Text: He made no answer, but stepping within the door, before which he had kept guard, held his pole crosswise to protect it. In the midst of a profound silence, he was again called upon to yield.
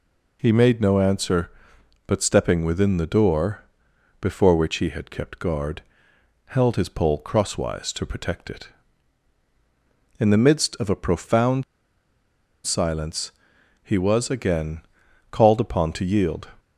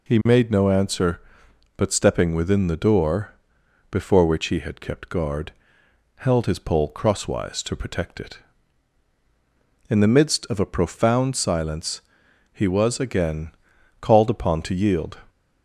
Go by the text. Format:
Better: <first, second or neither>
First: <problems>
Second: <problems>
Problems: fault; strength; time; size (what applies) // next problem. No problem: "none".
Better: second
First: pauses between "profound" and "silence"; at 11.6 s; 1.0 s long // pauses between "again" and "called"; noticeable; at 14.8 s; 0.48 s long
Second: pauses between "again" and "called"; noticeable; at 13.5 s; 0.48 s long